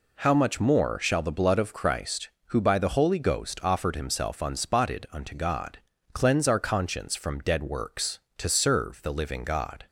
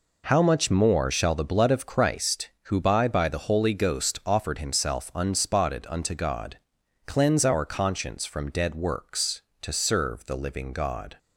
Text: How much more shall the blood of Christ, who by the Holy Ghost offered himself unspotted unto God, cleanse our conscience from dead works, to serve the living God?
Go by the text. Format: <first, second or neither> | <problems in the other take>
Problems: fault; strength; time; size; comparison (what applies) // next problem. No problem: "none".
first | says "by" twice; at 3.0 s